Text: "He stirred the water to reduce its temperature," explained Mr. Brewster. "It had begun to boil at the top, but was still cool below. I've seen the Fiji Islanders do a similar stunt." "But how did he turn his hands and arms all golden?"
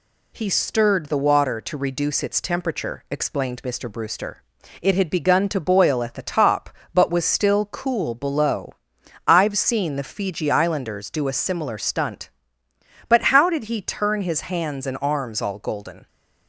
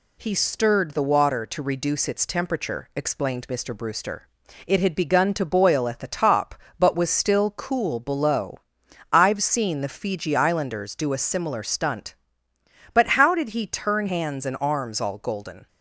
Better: first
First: none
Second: skips "his"; at 14.0 s

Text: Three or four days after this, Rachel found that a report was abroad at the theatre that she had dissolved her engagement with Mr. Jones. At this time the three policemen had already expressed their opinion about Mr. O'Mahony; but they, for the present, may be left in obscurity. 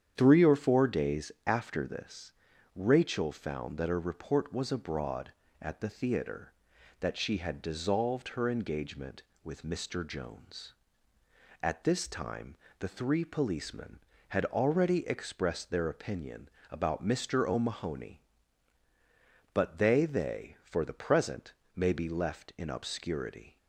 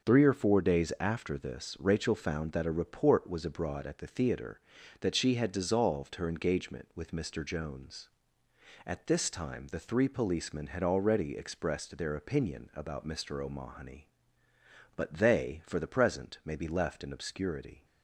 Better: second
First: starts louder than the rest; strong; until 1.1 s; 8.5 dB // pauses between "days" and "after"; slight; at 1.2 s; 0.16 s long // pauses between "time" and "the"; slight; at 12.5 s; 0.24 s long // pauses between "opinion" and "about"; slight; at 16.4 s; 0.22 s long // says "they" twice; at 20.0 s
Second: starts louder than the rest; until 1.1 s; 6.5 dB

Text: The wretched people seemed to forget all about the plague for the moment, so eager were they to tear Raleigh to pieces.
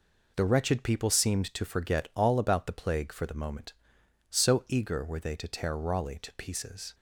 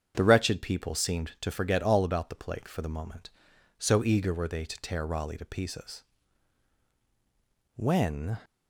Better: first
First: none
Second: starts louder than the rest; strong; until 1.1 s; 7.5 dB // goes on to say "When"; noticeable; from 7.7 s on; 0.62 s long

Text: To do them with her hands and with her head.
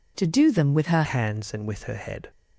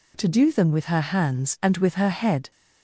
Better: second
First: changes voice at "hands"; from 1.0 s on; 1.3 s long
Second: none

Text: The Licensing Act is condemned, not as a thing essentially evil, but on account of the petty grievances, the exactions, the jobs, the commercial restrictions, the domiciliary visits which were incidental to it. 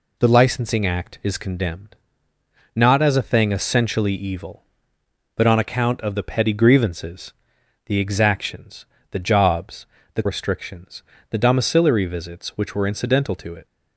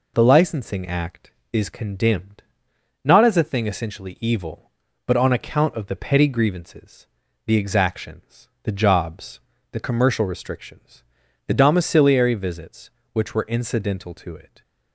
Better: second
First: skips "commercial"; at 10.2 s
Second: none

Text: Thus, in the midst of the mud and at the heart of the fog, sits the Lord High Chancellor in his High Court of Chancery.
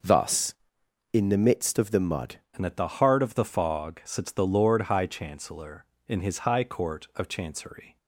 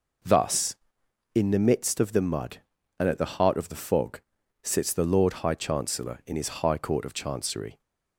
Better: second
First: changes voice at "and"; from 2.5 s on; 5.4 s long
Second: none

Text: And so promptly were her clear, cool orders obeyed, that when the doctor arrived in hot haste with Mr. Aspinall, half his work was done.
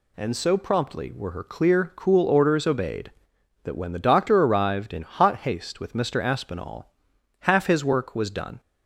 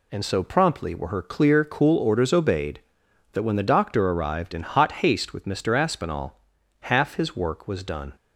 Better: neither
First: none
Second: none

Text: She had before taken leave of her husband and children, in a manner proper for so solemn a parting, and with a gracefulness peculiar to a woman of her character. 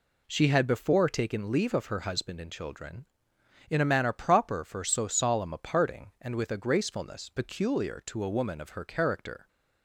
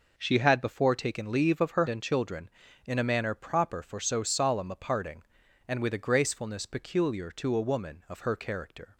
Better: first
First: none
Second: skips "husband"; at 1.8 s

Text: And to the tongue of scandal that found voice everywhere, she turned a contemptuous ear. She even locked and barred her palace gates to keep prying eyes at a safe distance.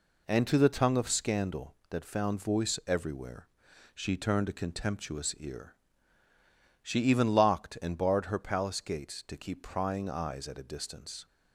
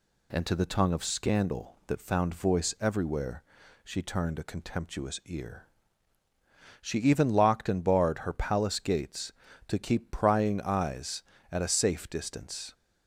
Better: second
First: skips "safe"; at 10.6 s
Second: none

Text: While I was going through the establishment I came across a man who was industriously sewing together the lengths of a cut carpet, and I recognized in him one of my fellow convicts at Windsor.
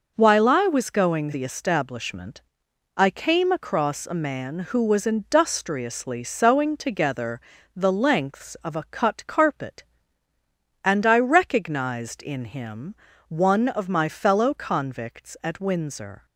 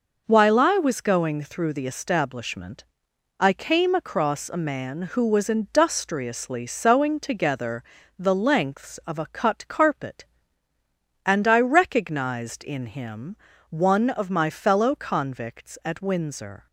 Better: second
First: skips "through"; at 1.3 s // pauses between "establishment" and "I"; noticeable; at 2.4 s; 0.54 s long // pauses between "together" and "the"; slight; at 7.4 s; 0.34 s long // pauses between "him" and "one"; slight; at 12.9 s; 0.34 s long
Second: pauses between "establishment" and "I"; noticeable; at 2.8 s; 0.54 s long // pauses between "together" and "the"; slight; at 7.8 s; 0.34 s long // pauses between "him" and "one"; slight; at 13.3 s; 0.34 s long

